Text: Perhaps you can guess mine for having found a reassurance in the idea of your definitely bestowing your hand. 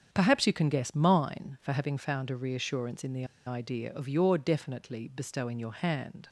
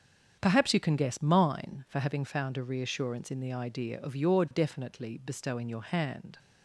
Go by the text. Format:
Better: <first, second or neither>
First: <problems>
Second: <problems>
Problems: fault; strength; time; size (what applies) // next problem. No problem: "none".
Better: second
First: starts louder than the rest; strong; until 1.1 s; 7.5 dB // pauses between "the" and "idea"; slight; at 3.2 s; 0.21 s long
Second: starts louder than the rest; strong; until 1.4 s; 7.5 dB